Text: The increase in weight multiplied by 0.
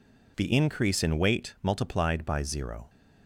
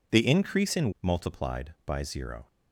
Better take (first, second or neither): first